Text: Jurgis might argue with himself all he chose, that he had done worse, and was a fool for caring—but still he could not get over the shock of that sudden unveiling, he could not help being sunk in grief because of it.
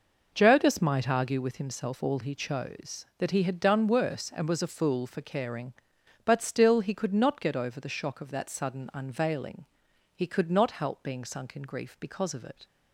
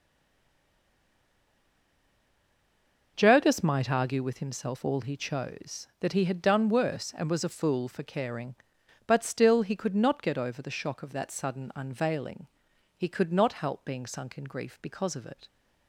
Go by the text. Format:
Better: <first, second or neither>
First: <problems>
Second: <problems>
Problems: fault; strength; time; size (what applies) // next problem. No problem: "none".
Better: first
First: none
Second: stays silent before the first word; strong; until 3.1 s; 3.1 s long